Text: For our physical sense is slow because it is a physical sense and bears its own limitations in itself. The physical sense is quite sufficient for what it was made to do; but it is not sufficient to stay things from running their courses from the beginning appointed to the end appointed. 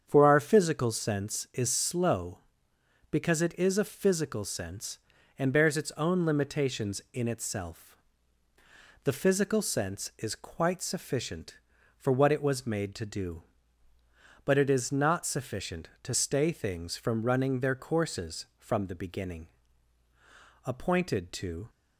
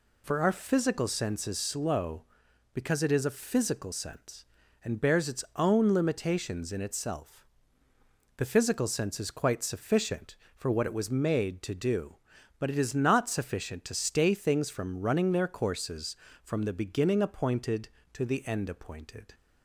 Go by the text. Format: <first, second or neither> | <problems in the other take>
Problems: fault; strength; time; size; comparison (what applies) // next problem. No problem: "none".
second | starts louder than the rest; strong; until 1.0 s; 8 dB // pauses between "beginning" and "appointed"; at 19.4 s; 1.1 s long // stops before "the end appointed"; at 21.6 s